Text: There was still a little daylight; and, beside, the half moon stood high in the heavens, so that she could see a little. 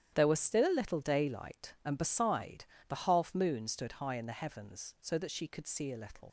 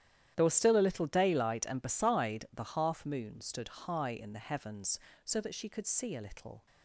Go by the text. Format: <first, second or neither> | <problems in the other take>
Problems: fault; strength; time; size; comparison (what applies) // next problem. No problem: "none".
second | starts louder than the rest; strong; until 1.1 s; 10.5 dB; strong in the second // leaves "little" unfinished; at 6.2 s; 85 ms